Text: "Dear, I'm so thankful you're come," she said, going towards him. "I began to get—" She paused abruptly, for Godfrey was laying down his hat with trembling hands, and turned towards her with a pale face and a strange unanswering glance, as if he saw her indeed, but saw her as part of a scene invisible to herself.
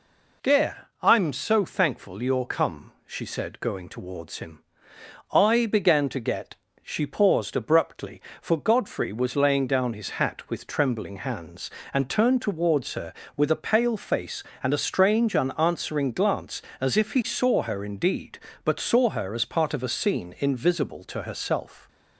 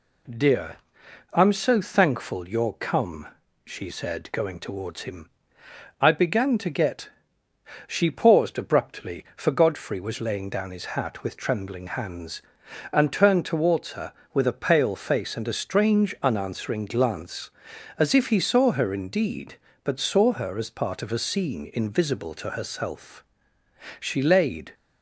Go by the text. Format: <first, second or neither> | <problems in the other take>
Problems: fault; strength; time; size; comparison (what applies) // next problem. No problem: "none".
first | goes on to say "She laid"; noticeable; from 23.9 s on; 0.74 s long